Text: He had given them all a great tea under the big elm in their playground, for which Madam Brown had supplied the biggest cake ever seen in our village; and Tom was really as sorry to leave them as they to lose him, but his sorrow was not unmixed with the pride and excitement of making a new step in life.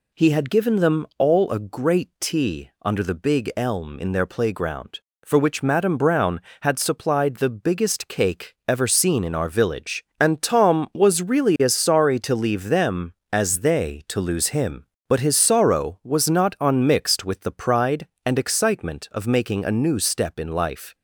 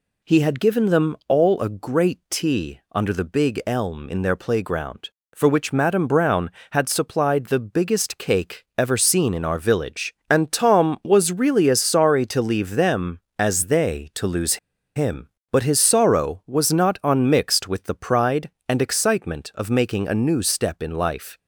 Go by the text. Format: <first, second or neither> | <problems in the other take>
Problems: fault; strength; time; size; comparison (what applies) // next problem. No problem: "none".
first | pauses between "lose" and "him"; at 14.5 s; 0.36 s long